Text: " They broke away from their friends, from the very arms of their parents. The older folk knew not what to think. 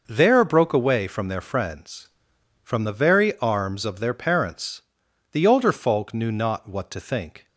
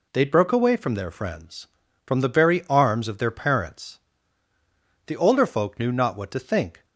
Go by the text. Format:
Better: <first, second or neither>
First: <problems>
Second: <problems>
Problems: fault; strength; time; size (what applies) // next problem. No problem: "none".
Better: second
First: says "There" for "They"; at 0.0 s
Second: none